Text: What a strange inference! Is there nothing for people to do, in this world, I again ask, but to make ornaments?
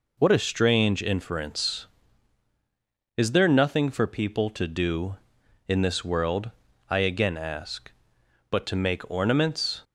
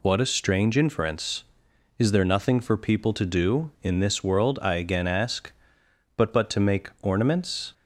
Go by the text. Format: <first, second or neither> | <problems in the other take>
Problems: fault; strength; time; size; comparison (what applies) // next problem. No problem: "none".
first | says "but" twice; at 6.3 s